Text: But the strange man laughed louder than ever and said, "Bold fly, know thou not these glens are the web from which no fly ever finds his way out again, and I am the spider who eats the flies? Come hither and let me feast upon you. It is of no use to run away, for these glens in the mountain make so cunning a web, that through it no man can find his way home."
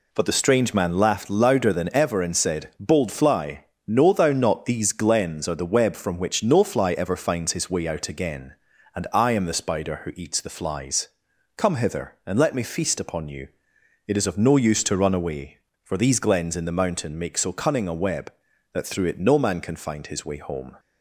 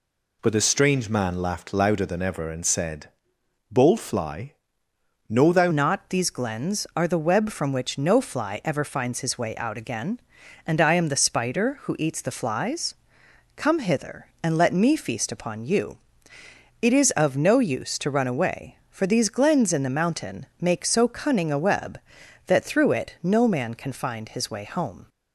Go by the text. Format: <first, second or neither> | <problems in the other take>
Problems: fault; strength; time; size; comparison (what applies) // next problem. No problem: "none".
first | changes voice at "not"; from 5.7 s on; 19.3 s long